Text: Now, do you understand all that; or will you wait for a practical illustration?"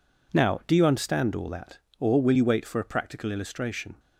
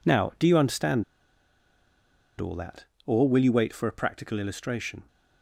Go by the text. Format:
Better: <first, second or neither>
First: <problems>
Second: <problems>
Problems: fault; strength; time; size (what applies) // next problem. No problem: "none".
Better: first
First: none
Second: pauses between "understand" and "all"; strong; at 1.0 s; 1.3 s long